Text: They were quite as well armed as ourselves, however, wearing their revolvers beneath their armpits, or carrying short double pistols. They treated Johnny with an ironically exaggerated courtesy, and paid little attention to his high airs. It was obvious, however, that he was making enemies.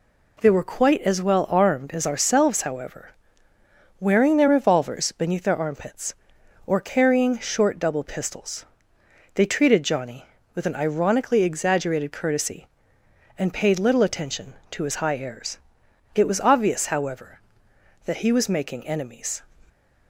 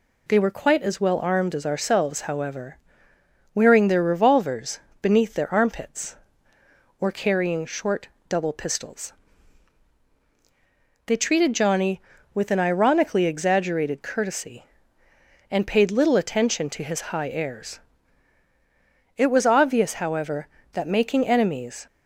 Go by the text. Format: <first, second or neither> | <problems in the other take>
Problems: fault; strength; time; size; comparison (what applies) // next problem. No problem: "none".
first | pauses between "revolvers" and "beneath"; slight; at 4.7 s; 0.22 s long // pauses between "short" and "double"; slight; at 8.0 s; 0.20 s long // skips "he was"; at 20.8 s